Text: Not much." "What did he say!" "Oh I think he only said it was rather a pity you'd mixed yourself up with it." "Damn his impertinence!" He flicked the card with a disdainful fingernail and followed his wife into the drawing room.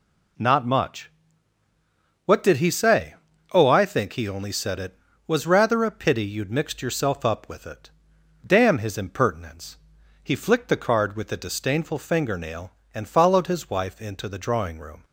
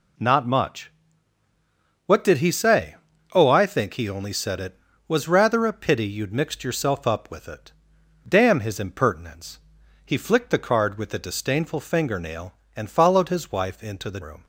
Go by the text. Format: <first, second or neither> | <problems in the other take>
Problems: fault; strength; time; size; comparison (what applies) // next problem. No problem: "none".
first | skips "drawing"; at 14.2 s